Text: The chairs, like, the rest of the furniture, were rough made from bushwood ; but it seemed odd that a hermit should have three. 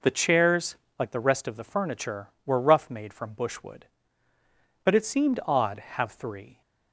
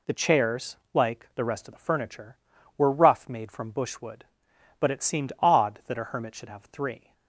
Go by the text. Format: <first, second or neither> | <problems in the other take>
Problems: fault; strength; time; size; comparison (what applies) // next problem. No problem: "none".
second | skips "that a hermit should"; at 5.7 s